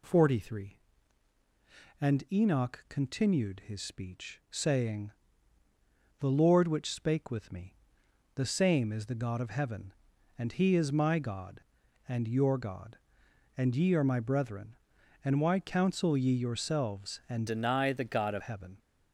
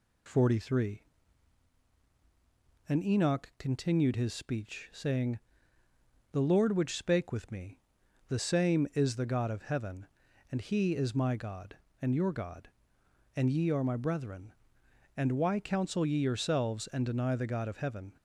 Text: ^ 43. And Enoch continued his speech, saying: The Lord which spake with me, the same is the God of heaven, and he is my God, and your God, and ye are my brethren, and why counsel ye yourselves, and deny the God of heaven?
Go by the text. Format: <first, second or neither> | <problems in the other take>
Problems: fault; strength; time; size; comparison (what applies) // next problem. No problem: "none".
second | changes voice from "deny" to "of"; from 17.4 to 18.4 s; 1.0 s long